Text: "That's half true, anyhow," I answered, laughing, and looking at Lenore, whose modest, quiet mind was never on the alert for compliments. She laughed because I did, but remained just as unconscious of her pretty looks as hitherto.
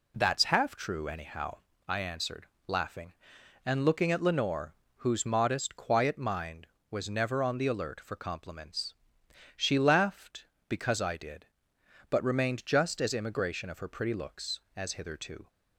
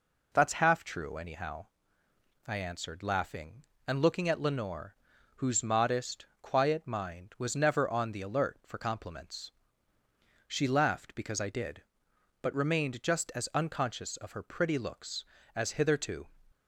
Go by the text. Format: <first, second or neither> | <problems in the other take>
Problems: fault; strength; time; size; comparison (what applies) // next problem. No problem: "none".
second | says "immigration" for "unconscious"; at 13.1 s